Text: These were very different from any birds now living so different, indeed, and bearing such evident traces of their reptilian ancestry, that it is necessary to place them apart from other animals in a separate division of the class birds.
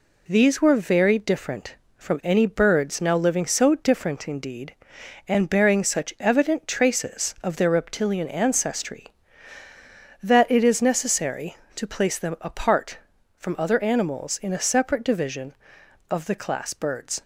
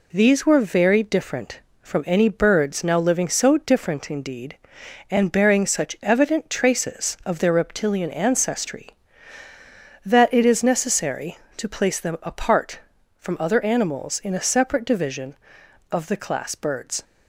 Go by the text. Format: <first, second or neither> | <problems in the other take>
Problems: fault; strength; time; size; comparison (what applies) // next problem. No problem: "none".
neither | none